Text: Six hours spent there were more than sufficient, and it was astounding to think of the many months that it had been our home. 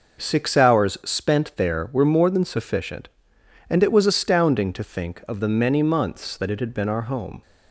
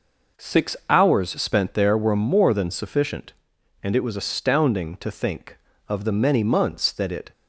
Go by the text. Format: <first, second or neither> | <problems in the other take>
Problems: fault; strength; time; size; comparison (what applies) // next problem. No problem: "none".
first | stops before "had been our home"; at 7.3 s